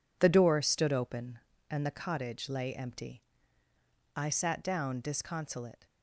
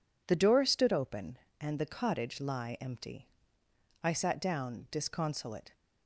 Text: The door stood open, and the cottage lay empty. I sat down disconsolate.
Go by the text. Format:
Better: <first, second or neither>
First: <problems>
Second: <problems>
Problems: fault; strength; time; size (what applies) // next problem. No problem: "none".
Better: first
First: none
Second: says "lie" for "lay"; at 2.4 s